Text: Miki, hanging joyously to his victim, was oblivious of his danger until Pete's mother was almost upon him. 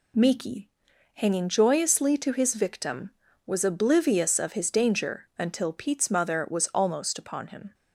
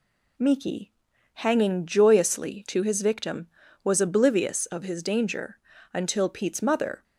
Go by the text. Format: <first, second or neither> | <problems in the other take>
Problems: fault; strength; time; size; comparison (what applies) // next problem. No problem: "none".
first | pauses between "danger" and "until"; slight; at 5.5 s; 0.36 s long // stops before "was almost upon him"; at 7.0 s